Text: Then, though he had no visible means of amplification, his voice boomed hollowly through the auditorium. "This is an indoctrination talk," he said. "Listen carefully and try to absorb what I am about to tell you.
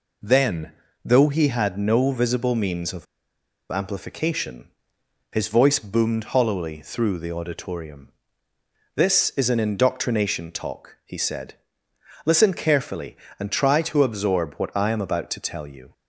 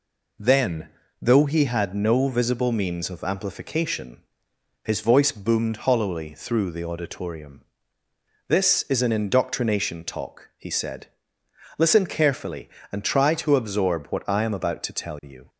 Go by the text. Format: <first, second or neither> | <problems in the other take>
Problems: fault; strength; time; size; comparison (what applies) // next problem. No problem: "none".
second | pauses between "of" and "amplification"; noticeable; at 3.0 s; 0.65 s long